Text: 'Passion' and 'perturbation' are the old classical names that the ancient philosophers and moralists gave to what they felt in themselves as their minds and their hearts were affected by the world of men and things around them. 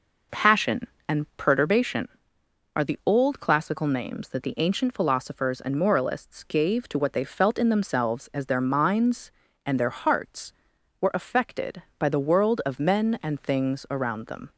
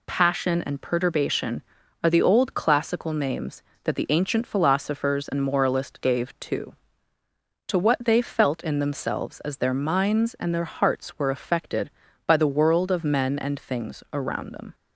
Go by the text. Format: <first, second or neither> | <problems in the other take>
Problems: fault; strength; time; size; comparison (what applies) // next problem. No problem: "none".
first | says "to" twice; at 7.6 s